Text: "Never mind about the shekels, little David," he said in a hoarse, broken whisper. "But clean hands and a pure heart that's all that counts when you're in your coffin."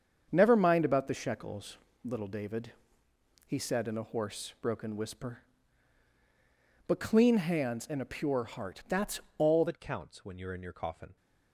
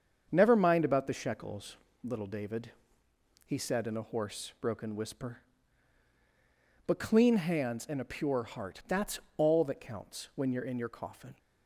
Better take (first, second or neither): second